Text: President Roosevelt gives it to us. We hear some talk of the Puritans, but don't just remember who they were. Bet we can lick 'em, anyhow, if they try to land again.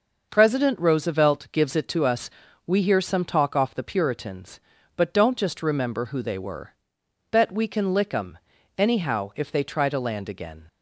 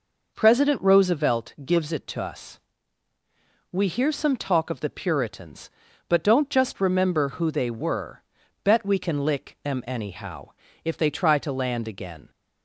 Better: second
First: says "off" for "of"; at 3.5 s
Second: none

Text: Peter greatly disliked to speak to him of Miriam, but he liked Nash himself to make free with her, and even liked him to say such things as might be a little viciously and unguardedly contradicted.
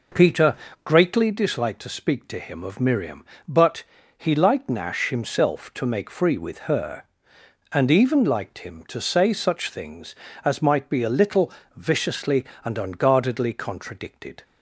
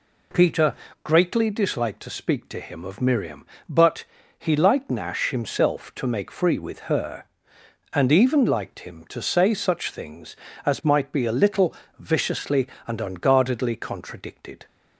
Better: second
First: starts louder than the rest; noticeable; until 1.4 s; 5 dB // pauses between "Peter" and "greatly"; slight; at 0.5 s; 0.30 s long // pauses between "but" and "he"; slight; at 3.8 s; 0.34 s long // pauses between "little" and "viciously"; slight; at 11.5 s; 0.26 s long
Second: pauses between "Peter" and "greatly"; slight; at 0.7 s; 0.30 s long // pauses between "but" and "he"; slight; at 4.0 s; 0.34 s long // pauses between "little" and "viciously"; slight; at 11.7 s; 0.26 s long

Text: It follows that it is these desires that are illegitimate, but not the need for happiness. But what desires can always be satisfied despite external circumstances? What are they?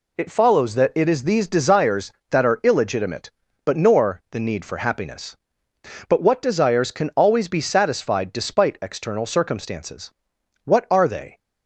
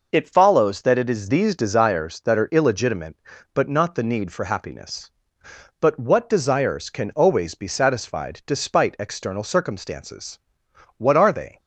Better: second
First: says "nor" for "not"; at 3.7 s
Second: none

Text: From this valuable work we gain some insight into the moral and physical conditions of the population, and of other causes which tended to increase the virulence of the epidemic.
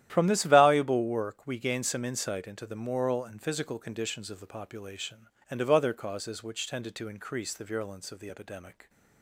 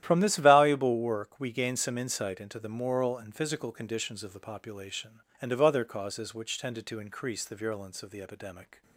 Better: neither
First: starts louder than the rest; strong; until 1.1 s; 11.5 dB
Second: starts louder than the rest; strong; until 1.0 s; 11.5 dB

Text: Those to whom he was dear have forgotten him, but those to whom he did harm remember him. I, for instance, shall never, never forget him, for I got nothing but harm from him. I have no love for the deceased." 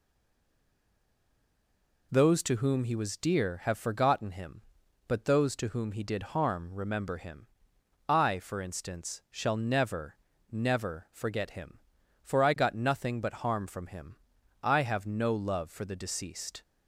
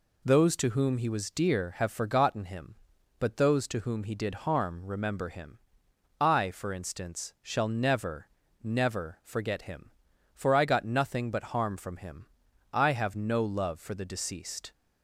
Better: second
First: stays silent before the first word; noticeable; until 2.1 s; 2.1 s long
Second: none

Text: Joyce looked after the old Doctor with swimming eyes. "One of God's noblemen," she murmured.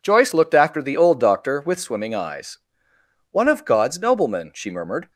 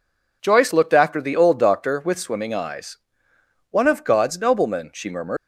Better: first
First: none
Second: leaves "murmured" unfinished; at 5.3 s; 130 ms

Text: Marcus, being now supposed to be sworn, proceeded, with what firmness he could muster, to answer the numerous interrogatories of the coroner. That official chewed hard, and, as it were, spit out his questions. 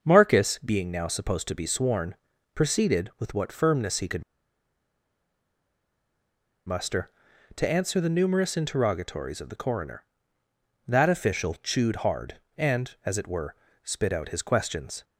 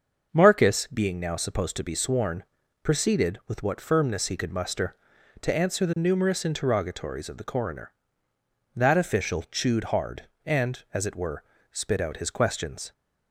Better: second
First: starts louder than the rest; until 1.0 s; 6.5 dB // pauses between "could" and "muster"; strong; at 4.2 s; 2.4 s long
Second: starts louder than the rest; until 1.3 s; 6.5 dB

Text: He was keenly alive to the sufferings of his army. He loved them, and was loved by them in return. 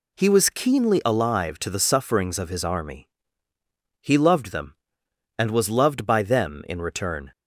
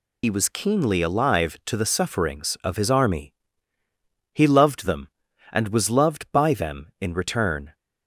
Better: first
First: none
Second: loses the start of "He"; at 0.2 s; 70 ms

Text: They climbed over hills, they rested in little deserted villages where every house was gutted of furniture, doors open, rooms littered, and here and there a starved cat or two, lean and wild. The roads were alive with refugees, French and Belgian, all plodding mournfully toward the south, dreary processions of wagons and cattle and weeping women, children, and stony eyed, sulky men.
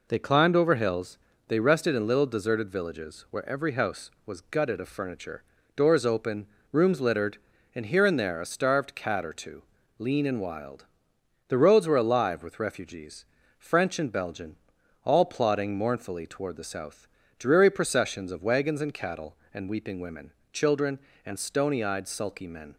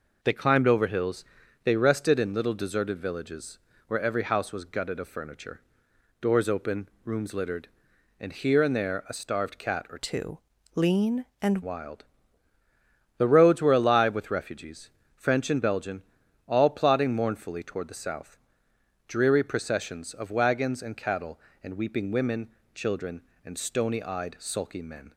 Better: first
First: none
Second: pauses between "villages" and "where"; slight; at 3.5 s; 0.30 s long // changes voice from "two" to "and"; from 9.9 to 11.6 s; 1.7 s long

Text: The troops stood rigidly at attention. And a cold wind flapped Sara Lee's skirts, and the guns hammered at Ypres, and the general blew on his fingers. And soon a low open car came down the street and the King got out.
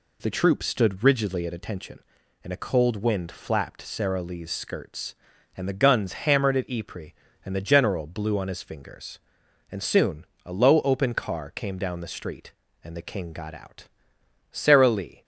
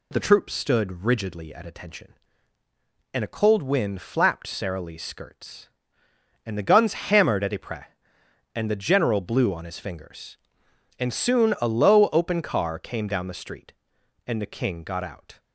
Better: second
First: pauses between "soon" and "a"; slight; at 10.2 s; 0.18 s long // goes on to say "Sara Lee"; noticeable; from 14.5 s on; 0.72 s long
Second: none

